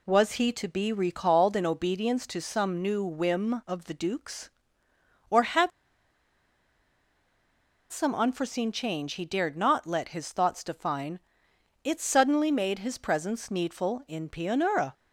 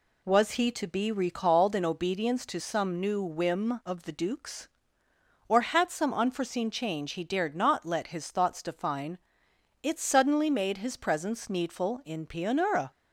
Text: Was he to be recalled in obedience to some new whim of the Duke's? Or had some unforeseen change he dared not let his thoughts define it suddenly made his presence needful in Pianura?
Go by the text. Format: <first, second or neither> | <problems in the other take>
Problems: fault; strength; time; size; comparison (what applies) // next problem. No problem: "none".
second | pauses between "had" and "some"; strong; at 5.7 s; 2.2 s long // pauses between "define" and "it"; noticeable; at 11.1 s; 0.64 s long; noticeable in the second